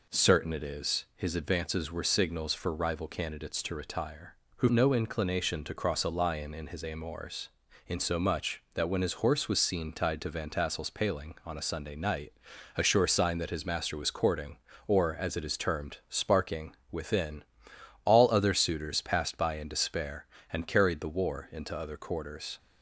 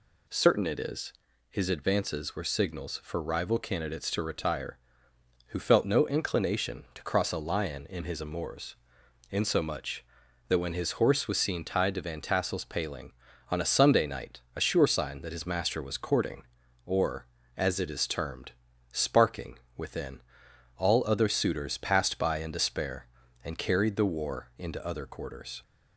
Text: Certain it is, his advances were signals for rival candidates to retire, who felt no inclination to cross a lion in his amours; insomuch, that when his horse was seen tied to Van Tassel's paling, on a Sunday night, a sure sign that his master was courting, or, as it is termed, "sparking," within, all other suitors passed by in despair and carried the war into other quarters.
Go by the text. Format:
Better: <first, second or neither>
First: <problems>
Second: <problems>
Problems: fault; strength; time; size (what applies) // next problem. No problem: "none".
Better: second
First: skips "felt"; at 4.7 s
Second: none